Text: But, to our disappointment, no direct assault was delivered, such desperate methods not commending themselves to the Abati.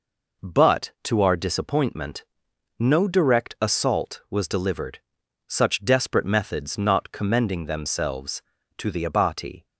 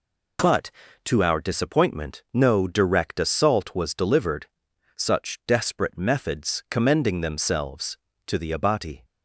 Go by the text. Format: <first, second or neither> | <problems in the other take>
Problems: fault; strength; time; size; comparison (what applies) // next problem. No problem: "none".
first | skips "not"; at 6.6 s